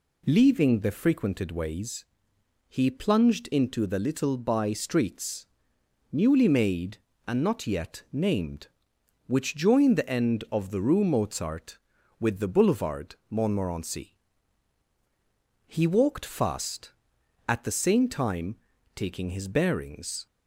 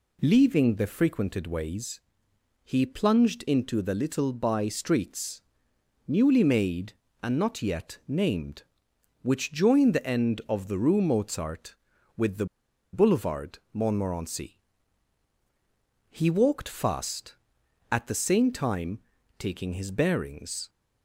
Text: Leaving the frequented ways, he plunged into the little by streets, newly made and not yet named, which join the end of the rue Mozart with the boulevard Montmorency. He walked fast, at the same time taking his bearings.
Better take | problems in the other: first | pauses between "the" and "boulevard"; noticeable; at 12.4 s; 0.47 s long // pauses between "boulevard" and "Montmorency"; slight; at 13.5 s; 0.16 s long; slight in the first // pauses between "time" and "taking"; at 18.9 s; 0.38 s long; also in the first

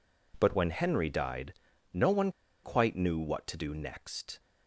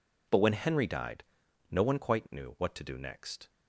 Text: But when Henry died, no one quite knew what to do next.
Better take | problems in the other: second | pauses between "one" and "quite"; slight; at 2.2 s; 0.34 s long

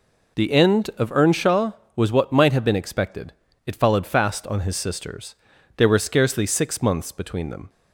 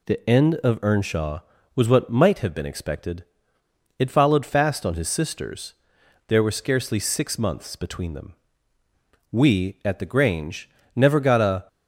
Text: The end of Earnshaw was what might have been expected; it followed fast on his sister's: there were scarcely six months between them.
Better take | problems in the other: first | goes on to say "We at the Grange never got a"; strong; from 9.3 s on; 2.3 s long

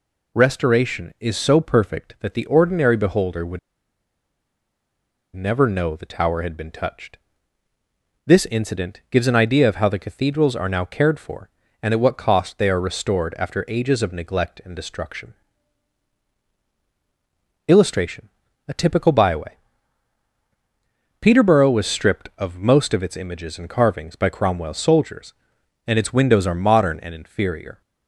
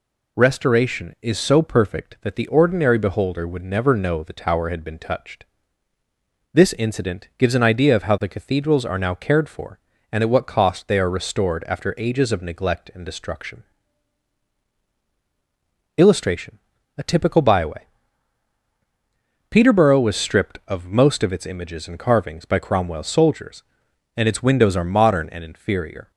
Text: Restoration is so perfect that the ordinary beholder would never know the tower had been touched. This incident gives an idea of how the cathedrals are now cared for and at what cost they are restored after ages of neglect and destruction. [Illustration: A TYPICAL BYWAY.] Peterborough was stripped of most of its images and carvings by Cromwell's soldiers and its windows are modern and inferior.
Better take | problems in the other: second | pauses between "would" and "never"; strong; at 3.5 s; 1.7 s long

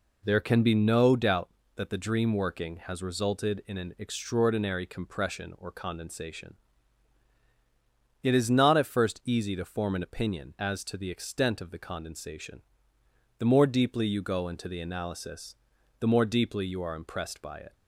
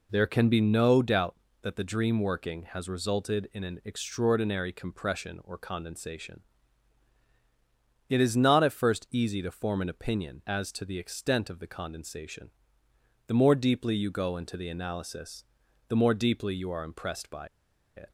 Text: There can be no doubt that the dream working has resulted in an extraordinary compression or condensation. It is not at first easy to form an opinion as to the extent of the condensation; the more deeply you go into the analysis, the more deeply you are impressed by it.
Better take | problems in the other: first | pauses between "by" and "it"; noticeable; at 17.4 s; 0.50 s long

